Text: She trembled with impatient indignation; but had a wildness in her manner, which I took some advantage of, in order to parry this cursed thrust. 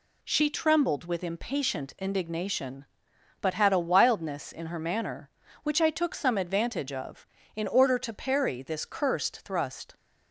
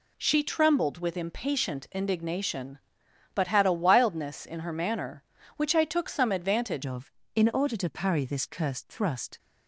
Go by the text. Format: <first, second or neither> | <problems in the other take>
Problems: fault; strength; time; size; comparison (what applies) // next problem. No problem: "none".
first | changes voice at "of"; from 6.8 s on; 2.5 s long